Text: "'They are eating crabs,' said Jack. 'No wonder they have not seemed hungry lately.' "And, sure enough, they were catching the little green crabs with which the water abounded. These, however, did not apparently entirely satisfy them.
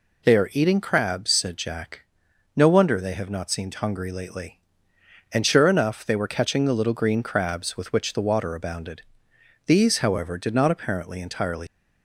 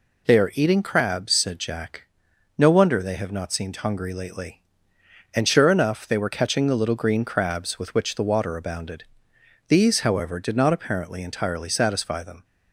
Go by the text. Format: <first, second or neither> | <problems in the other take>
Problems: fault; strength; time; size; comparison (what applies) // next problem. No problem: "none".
second | stops before "satisfy them"; at 11.6 s